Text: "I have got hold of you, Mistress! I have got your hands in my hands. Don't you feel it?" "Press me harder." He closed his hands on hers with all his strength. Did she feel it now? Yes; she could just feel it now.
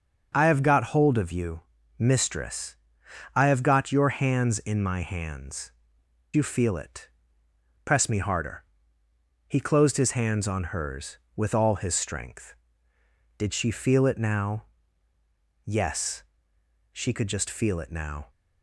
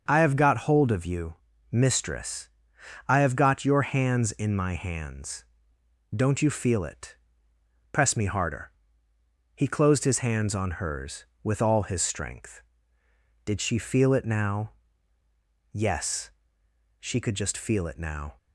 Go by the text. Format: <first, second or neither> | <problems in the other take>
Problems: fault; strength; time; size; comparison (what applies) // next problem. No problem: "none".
second | starts louder than the rest; until 1.3 s; 6 dB; also in the second // skips "Don't"; at 6.0 s